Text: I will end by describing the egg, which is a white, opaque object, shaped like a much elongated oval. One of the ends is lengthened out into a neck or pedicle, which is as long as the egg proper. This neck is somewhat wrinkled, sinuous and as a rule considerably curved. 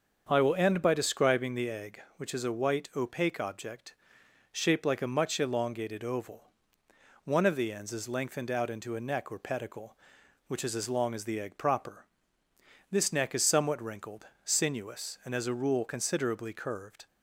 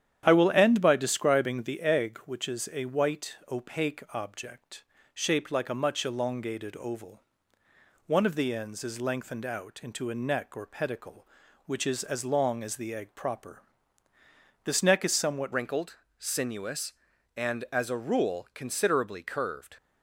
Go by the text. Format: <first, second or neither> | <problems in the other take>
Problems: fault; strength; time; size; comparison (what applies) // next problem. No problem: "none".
first | starts louder than the rest; strong; until 1.2 s; 10 dB; also in the first // changes voice at "wrinkled"; from 15.5 s on; 4.2 s long